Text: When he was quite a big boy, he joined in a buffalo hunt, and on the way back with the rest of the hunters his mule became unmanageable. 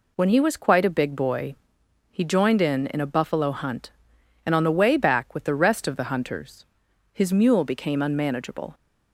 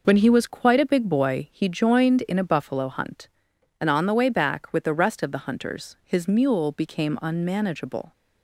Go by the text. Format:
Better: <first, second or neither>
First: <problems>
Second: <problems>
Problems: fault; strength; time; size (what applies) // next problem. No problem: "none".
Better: second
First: says "in" twice; at 2.9 s // pauses between "hunters" and "his"; noticeable; at 6.6 s; 0.48 s long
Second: none